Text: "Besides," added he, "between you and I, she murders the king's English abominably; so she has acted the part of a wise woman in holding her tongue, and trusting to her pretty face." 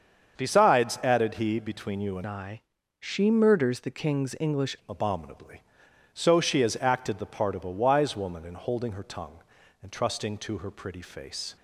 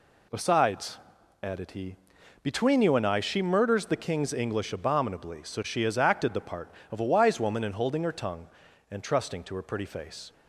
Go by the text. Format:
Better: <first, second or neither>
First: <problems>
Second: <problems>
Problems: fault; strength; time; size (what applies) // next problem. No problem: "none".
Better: second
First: starts louder than the rest; until 1.4 s; 7 dB // changes voice from "I" to "English"; from 2.2 to 4.7 s; 2.5 s long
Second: none